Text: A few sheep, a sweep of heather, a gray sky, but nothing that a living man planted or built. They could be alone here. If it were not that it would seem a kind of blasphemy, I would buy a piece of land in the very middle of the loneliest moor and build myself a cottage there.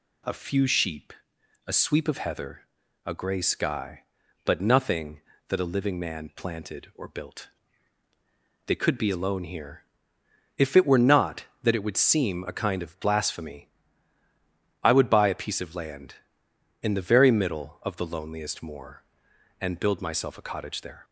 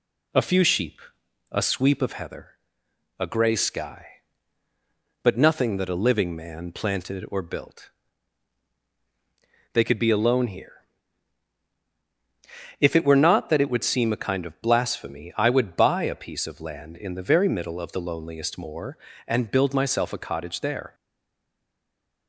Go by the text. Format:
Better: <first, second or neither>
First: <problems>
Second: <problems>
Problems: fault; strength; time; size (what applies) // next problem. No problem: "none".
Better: first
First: none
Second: stays silent after the last word; noticeable; from 20.9 s on; 1.3 s long